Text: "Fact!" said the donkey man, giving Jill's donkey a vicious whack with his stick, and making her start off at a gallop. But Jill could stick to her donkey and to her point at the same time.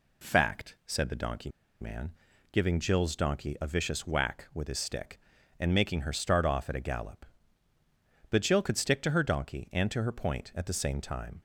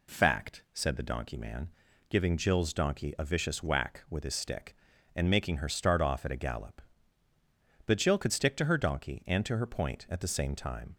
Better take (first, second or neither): second